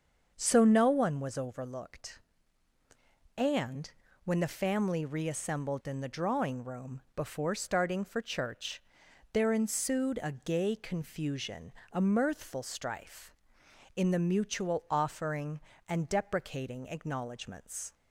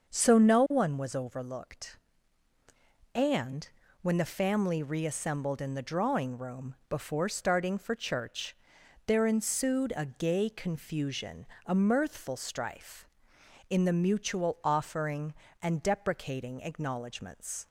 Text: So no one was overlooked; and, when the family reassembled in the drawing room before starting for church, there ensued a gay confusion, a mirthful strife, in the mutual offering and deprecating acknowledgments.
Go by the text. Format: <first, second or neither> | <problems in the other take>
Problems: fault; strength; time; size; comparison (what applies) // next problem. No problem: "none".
neither | starts louder than the rest; the same in both